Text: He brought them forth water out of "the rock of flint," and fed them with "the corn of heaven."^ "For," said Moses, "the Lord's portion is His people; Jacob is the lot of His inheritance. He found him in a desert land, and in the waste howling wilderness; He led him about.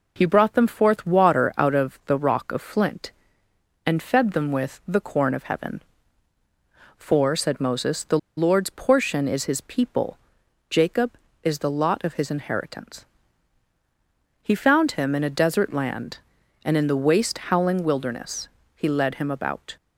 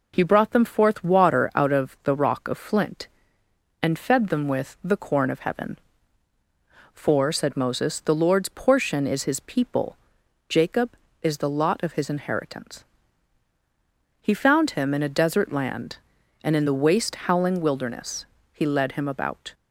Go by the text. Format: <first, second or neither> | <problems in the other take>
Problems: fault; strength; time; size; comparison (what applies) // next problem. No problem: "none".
second | pauses between "the" and "Lord's"; slight; at 8.1 s; 0.20 s long